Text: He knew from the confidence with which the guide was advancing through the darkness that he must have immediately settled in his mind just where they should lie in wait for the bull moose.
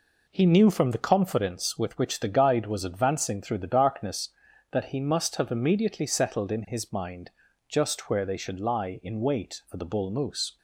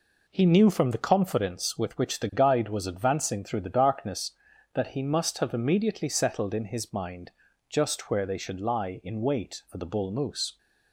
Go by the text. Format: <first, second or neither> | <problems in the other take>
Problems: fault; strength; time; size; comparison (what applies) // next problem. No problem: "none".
neither | pauses between "mind" and "just"; slight; the same in both